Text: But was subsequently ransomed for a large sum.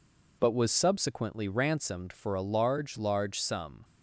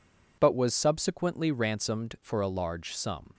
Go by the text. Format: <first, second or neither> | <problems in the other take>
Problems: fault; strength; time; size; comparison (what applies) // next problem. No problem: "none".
second | says "large" twice; at 2.9 s